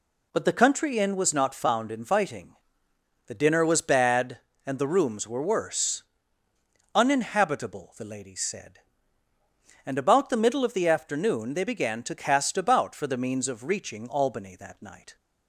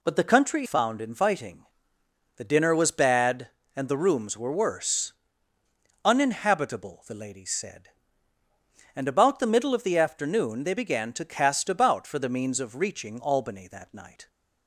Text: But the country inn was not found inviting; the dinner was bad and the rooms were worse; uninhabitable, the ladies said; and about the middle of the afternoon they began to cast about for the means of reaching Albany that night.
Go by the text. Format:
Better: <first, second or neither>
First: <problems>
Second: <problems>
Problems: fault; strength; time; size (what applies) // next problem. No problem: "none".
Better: first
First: none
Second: skips "inn was not"; at 0.6 s